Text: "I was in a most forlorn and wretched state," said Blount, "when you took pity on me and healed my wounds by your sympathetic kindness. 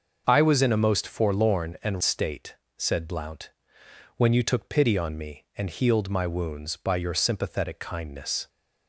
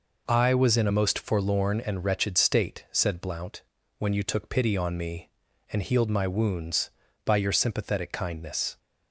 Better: second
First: starts louder than the rest; until 1.2 s; 6.5 dB // skips "wretched"; at 2.0 s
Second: none

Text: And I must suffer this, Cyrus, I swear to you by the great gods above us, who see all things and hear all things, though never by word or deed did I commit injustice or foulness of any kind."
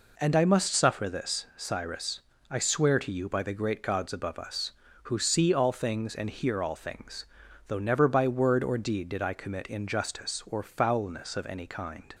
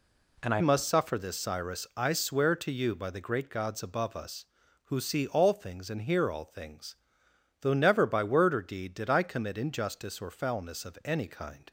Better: first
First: none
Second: changes voice at "must"; from 0.5 s on; 11.1 s long

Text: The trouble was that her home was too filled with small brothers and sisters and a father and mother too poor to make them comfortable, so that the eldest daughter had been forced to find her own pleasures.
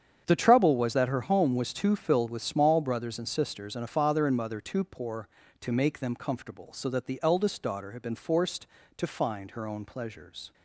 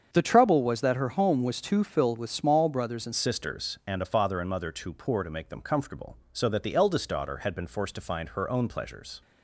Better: first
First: starts louder than the rest; strong; until 1.2 s; 8 dB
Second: starts louder than the rest; strong; until 1.1 s; 7.5 dB // changes voice at "sisters"; from 3.1 s on; 6.1 s long

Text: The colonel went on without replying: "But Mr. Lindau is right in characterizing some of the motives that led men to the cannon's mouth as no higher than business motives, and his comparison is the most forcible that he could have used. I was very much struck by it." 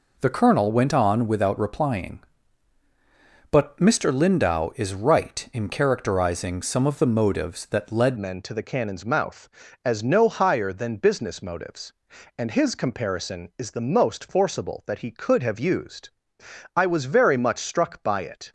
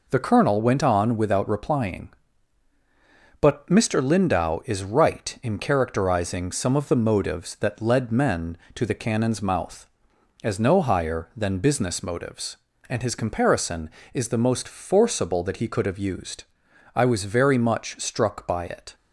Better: second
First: changes voice at "men"; from 8.1 s on; 10.4 s long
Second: none

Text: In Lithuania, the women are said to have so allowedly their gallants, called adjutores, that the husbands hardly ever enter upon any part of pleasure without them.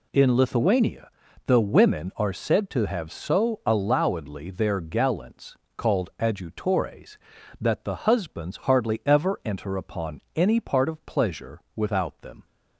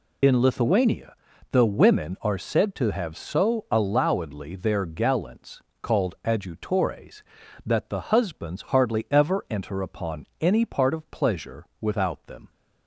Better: first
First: none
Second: loses the start of "In"; at 0.2 s; 70 ms

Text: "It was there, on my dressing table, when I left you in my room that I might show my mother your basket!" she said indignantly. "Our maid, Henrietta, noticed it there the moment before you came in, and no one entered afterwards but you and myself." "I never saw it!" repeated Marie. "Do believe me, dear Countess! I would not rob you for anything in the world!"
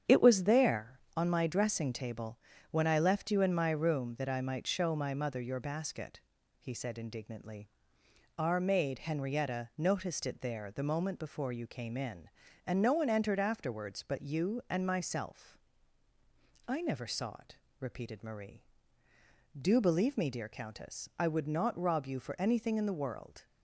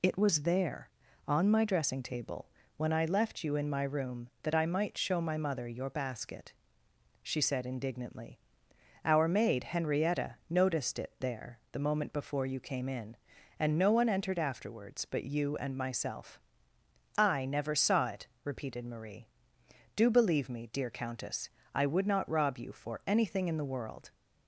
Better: second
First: starts louder than the rest; strong; until 1.2 s; 8.5 dB // says "he" for "she"; at 6.5 s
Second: none

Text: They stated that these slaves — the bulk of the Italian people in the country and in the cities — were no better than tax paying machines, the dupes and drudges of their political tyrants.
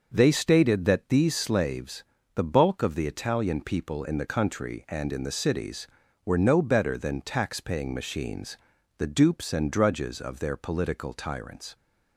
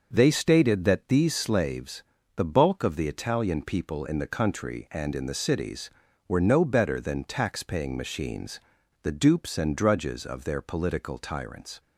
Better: neither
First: none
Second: none

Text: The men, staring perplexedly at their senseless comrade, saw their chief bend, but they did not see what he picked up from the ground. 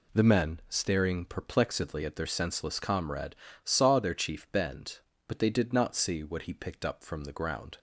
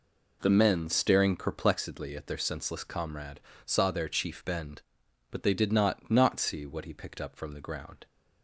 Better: first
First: none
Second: says "not" twice; at 6.0 s

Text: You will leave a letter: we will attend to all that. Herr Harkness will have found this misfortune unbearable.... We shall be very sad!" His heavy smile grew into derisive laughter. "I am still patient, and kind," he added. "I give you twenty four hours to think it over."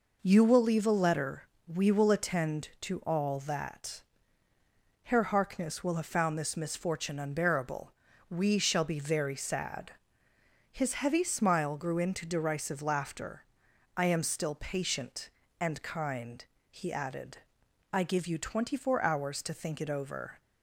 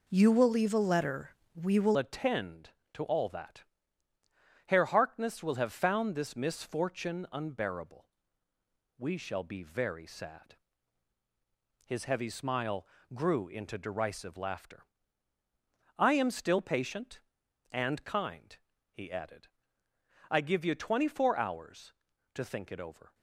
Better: first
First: none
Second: changes voice at "attend"; from 1.9 s on; 21.2 s long // pauses between "smile" and "grew"; slight; at 12.8 s; 0.30 s long

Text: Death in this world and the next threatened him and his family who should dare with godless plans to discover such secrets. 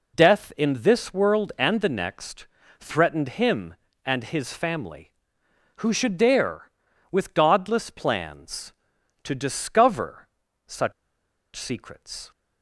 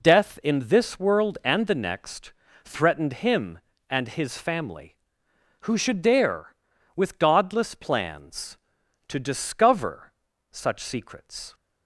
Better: second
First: pauses between "next" and "threatened"; slight; at 2.4 s; 0.34 s long // pauses between "discover" and "such"; at 10.2 s; 0.38 s long // pauses between "such" and "secrets"; noticeable; at 10.9 s; 0.63 s long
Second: pauses between "next" and "threatened"; slight; at 2.3 s; 0.32 s long // pauses between "discover" and "such"; at 10.1 s; 0.38 s long

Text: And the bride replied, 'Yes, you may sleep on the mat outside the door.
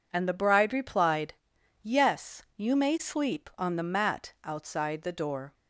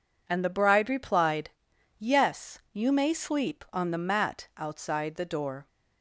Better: neither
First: none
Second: none

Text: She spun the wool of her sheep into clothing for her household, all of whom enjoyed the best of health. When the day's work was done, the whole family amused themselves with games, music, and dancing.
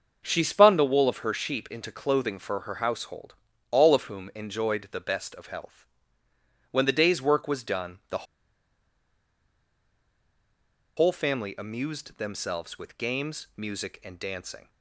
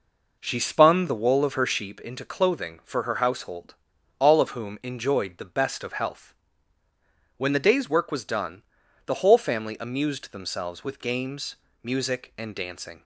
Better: second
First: starts louder than the rest; until 1.2 s; 6.5 dB // pauses between "the" and "whole"; strong; at 8.2 s; 2.7 s long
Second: none

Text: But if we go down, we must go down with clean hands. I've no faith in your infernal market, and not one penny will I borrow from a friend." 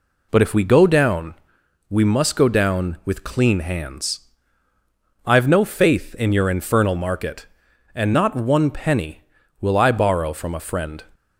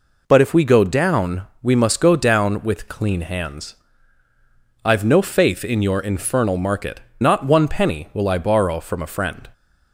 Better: first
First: none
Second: skips "and"; at 7.1 s

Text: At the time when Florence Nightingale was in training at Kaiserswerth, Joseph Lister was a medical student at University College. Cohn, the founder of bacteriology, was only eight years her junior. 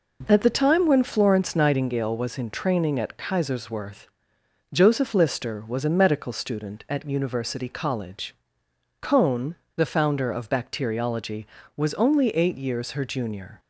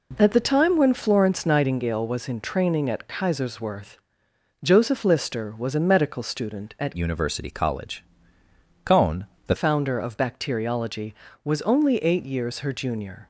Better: first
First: none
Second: changes voice from "University" to "the"; from 6.9 to 9.5 s; 2.6 s long

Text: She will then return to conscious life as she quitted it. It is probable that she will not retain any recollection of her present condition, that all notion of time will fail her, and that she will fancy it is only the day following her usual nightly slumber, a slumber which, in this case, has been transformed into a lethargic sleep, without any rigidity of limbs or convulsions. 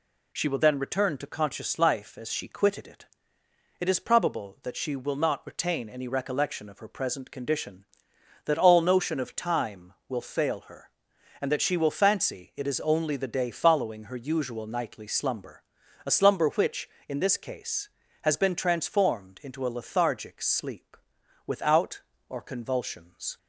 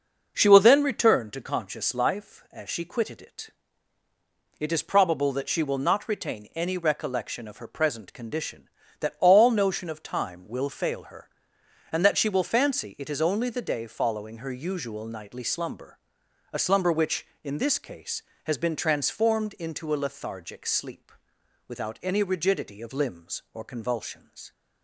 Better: second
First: skips "any rigidity of limbs"; at 22.1 s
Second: none

